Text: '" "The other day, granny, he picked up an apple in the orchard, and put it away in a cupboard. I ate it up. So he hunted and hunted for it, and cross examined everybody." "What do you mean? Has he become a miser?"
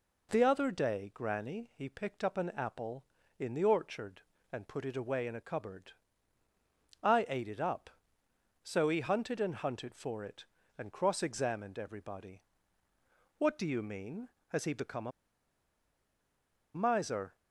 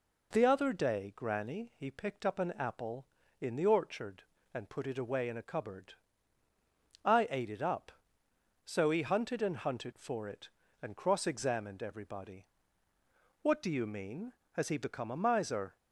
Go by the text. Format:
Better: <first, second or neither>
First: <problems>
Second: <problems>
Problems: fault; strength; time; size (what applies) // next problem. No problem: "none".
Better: second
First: pauses between "a" and "miser"; strong; at 15.1 s; 1.6 s long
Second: none